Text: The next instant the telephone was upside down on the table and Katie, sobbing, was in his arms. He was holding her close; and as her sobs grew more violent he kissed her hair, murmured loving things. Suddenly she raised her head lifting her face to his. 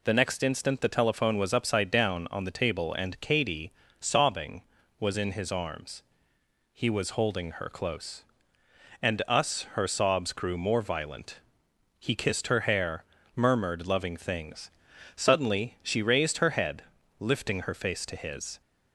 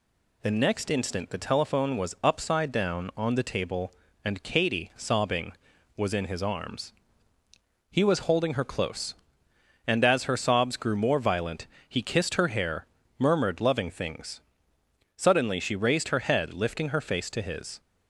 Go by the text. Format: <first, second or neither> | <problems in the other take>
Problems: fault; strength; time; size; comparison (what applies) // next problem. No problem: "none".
second | says "us" for "as"; at 9.2 s // pauses between "violent" and "he"; noticeable; at 11.4 s; 0.58 s long; slight in the second // pauses between "head" and "lifting"; slight; at 16.8 s; 0.36 s long